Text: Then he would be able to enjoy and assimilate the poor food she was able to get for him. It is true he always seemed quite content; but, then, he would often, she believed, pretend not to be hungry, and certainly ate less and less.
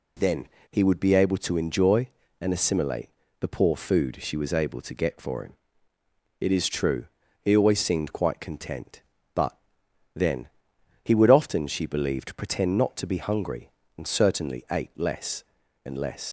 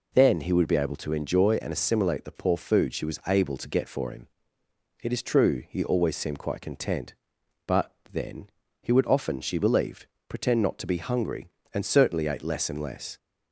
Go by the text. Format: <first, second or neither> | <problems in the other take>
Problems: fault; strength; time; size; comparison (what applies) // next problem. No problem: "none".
second | pauses between "Then" and "he"; slight; at 0.4 s; 0.22 s long // pauses between "assimilate" and "the"; slight; at 3.0 s; 0.30 s long // pauses between "true" and "he"; at 7.0 s; 0.38 s long // leaves "less" unfinished; at 16.2 s; 80 ms